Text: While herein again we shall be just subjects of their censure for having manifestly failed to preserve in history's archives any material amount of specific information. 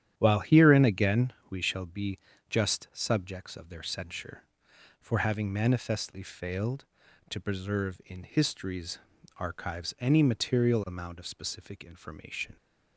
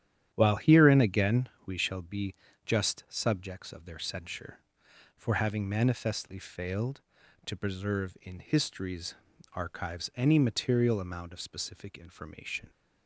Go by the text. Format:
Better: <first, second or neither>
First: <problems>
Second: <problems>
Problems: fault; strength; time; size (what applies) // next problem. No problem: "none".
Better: neither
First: starts louder than the rest; strong; until 1.1 s; 10 dB // pauses between "again" and "we"; slight; at 1.3 s; 0.16 s long // pauses between "be" and "just"; slight; at 2.1 s; 0.32 s long // pauses between "history's" and "archives"; at 8.9 s; 0.40 s long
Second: starts louder than the rest; strong; until 1.3 s; 10 dB // pauses between "again" and "we"; slight; at 1.4 s; 0.16 s long // pauses between "be" and "just"; slight; at 2.3 s; 0.32 s long // pauses between "history's" and "archives"; at 9.1 s; 0.40 s long